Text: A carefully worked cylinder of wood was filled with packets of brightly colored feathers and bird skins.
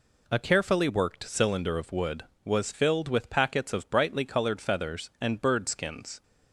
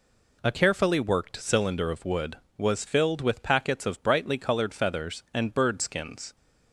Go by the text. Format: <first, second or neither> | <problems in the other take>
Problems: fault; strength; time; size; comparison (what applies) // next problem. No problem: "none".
neither | none